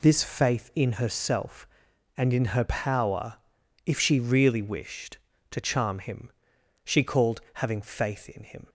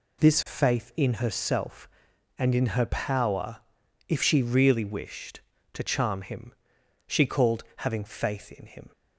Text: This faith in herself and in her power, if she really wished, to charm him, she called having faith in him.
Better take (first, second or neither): neither